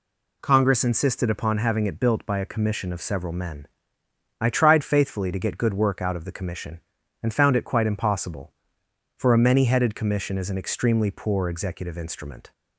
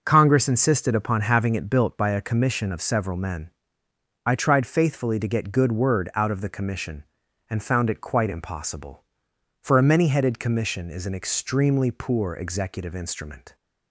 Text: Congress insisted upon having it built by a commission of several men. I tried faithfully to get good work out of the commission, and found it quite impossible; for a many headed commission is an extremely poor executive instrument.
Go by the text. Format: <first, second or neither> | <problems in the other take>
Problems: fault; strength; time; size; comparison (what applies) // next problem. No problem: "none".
first | says "word" for "work"; at 5.7 s